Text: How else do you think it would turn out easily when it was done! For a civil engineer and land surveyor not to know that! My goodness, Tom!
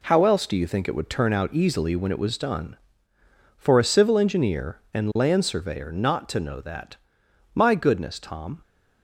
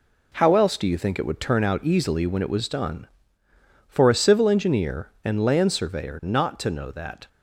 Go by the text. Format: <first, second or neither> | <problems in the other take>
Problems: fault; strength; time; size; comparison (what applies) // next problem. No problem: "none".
first | stops before "My goodness Tom"; at 7.2 s